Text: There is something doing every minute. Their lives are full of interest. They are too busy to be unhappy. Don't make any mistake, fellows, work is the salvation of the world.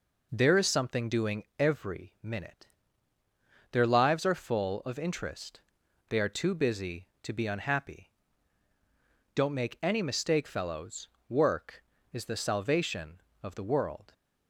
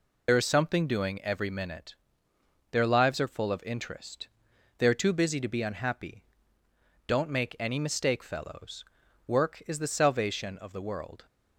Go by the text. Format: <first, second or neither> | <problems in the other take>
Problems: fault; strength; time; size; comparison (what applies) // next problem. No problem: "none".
first | loses the start of "There"; at 0.2 s; 65 ms